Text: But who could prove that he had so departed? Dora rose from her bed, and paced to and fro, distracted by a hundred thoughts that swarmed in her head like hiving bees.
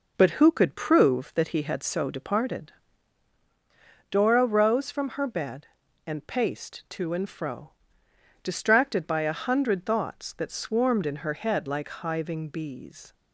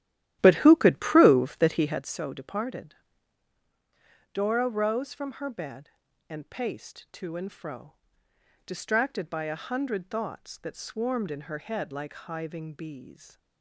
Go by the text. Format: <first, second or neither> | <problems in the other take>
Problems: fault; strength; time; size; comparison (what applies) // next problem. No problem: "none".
first | starts louder than the rest; strong; until 2.1 s; 13 dB